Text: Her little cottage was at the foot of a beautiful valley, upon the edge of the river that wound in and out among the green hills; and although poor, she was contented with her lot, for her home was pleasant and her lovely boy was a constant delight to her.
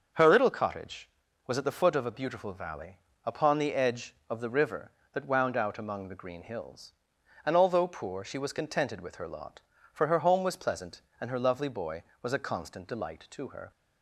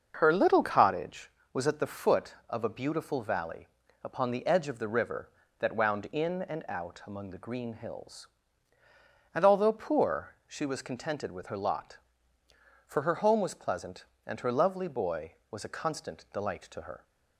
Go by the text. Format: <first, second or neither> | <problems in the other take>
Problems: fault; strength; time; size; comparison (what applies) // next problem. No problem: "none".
second | starts louder than the rest; noticeable; until 1.5 s; 6 dB; also in the second // skips "in and"; at 5.5 s